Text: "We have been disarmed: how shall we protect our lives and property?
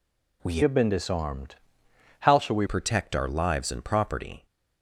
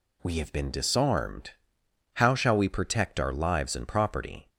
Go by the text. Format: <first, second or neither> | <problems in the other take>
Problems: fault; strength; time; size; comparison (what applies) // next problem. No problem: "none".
second | changes voice from "have" to "we"; from 0.6 to 2.6 s; 2.0 s long